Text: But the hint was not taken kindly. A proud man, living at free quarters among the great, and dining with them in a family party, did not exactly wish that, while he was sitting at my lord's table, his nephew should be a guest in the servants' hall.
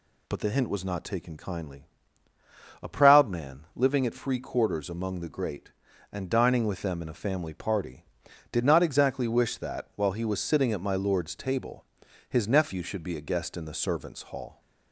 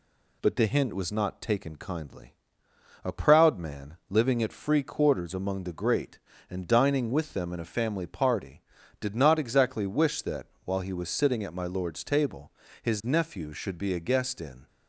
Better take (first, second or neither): first